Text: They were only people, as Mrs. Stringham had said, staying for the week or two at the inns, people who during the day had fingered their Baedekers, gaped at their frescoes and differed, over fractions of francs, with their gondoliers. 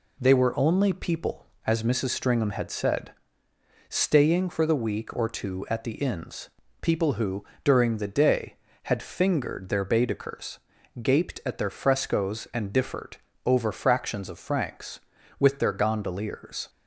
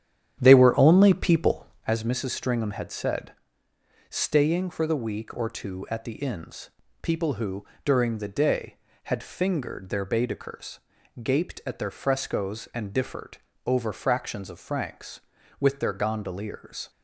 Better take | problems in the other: first | starts louder than the rest; strong; until 2.0 s; 9.5 dB // pauses between "who" and "during"; slight; at 7.6 s; 0.18 s long; slight in the first

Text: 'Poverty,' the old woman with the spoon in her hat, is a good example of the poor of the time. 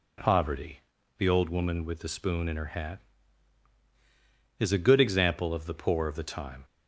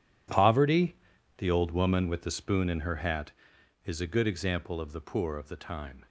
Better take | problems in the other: first | gets quieter; strong; throughout; 15.5 dB

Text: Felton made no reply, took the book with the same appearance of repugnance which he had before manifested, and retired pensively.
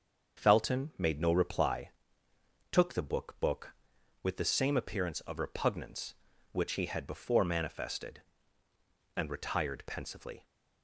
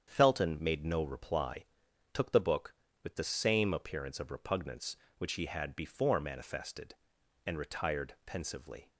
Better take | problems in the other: second | starts louder than the rest; until 1.4 s; 6.5 dB; strong in the second // says "book" twice; at 3.3 s

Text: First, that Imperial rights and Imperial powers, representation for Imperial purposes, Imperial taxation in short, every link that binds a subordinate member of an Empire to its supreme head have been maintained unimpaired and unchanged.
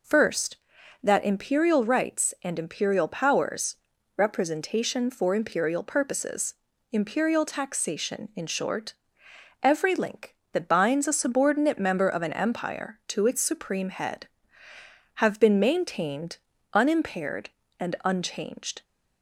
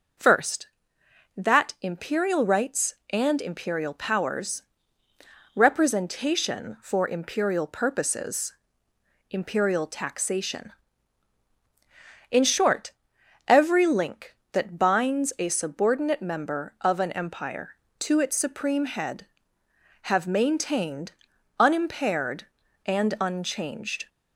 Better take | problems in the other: first | skips "been"; at 20.2 s // pauses between "maintained" and "unimpaired"; noticeable; at 21.1 s; 0.46 s long; slight in the first

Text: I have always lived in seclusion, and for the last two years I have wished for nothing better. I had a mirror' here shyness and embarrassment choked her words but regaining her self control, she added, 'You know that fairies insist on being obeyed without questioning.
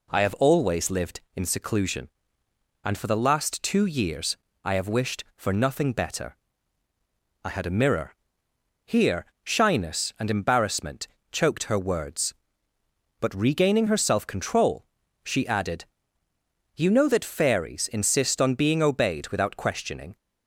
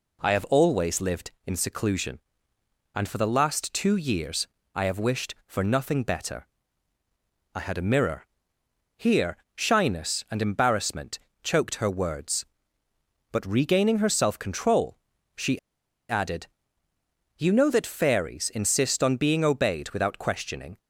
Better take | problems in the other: first | pauses between "years" and "I"; slight; at 4.4 s; 0.26 s long; slight in the first // pauses between "mirror" and "here"; noticeable; at 8.2 s; 0.70 s long; noticeable in the first // pauses between "here" and "shyness"; slight; at 9.3 s; 0.18 s long; slight in the first // pauses between "embarrassment" and "choked"; slight; at 11.1 s; 0.24 s long; slight in the first // pauses between "she" and "added"; noticeable; at 15.5 s; 0.51 s long

